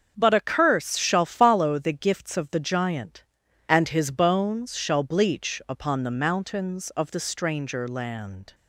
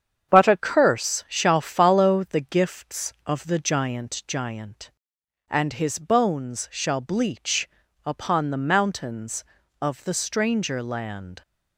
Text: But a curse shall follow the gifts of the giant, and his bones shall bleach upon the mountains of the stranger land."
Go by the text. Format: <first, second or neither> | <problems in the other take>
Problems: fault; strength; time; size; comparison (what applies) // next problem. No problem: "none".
first | starts louder than the rest; strong; until 1.3 s; 8 dB; also in the first // says "giant" twice; at 4.2 s // pauses between "bleach" and "upon"; at 7.6 s; 0.38 s long